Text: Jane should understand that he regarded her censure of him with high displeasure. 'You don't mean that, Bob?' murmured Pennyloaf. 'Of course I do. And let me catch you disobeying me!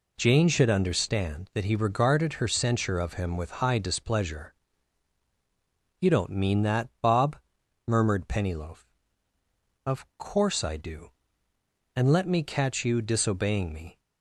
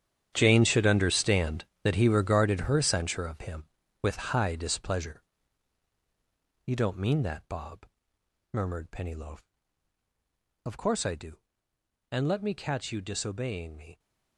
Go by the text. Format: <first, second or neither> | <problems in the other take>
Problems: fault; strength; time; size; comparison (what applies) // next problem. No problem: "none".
first | gets quieter; strong; throughout; 14 dB